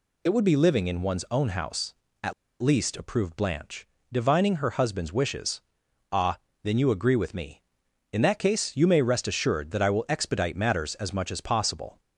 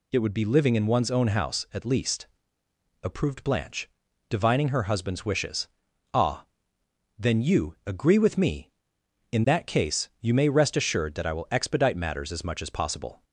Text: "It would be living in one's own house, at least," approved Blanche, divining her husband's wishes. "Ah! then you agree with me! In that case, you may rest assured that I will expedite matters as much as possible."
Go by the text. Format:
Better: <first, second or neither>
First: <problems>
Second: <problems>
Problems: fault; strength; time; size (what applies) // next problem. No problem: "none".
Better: second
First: pauses between "at" and "least"; slight; at 2.3 s; 0.29 s long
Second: none